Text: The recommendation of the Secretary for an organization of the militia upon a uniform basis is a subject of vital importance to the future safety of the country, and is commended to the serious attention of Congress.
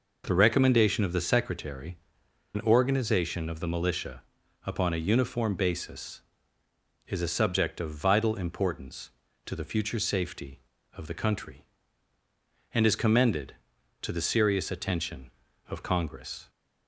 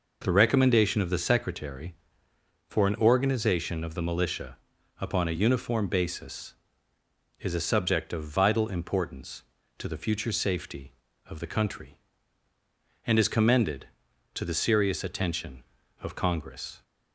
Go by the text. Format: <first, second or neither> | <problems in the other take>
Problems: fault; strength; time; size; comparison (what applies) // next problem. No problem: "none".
second | skips "for"; at 2.2 s // pauses between "militia" and "upon"; at 4.2 s; 0.44 s long; also in the second